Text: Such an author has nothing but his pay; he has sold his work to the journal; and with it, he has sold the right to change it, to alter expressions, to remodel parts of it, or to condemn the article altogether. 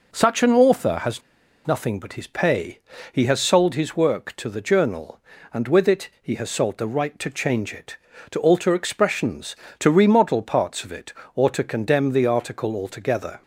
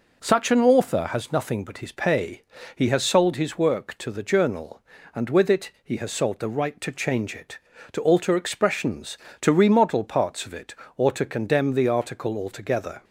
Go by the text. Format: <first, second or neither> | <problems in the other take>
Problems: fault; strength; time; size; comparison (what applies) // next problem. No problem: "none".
second | pauses between "has" and "nothing"; noticeable; at 1.2 s; 0.46 s long